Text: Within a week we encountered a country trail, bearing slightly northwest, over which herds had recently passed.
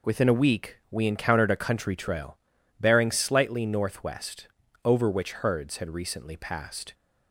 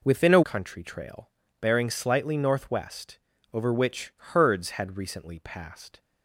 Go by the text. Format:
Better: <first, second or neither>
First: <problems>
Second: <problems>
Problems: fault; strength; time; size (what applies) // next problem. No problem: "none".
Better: first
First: none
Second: skips "week we encountered a"; at 0.4 s